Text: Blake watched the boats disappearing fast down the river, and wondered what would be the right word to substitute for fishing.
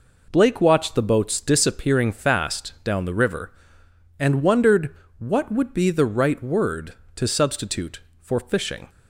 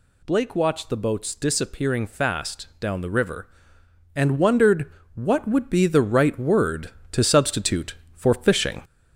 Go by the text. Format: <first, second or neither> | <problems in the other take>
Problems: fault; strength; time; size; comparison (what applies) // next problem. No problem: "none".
first | gets louder; slight; throughout; 3 dB // pauses between "wondered" and "what"; slight; at 4.8 s; 0.26 s long; slight in the first